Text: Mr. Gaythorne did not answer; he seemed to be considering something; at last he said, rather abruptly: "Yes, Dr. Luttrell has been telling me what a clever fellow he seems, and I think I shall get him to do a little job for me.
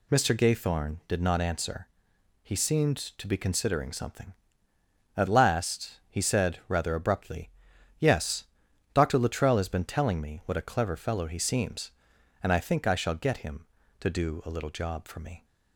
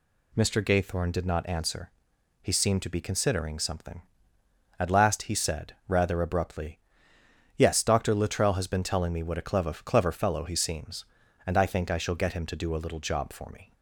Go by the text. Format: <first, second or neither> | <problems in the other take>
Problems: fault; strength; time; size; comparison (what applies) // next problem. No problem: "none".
first | says "clever" twice; at 9.7 s